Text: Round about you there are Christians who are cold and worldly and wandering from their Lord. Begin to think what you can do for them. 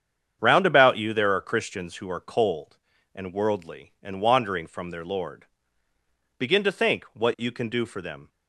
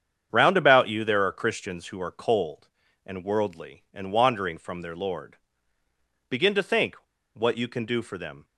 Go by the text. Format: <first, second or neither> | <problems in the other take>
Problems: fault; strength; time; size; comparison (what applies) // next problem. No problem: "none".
first | starts louder than the rest; strong; until 1.3 s; 8 dB; strong in the first // pauses between "think" and "what"; at 6.9 s; 0.39 s long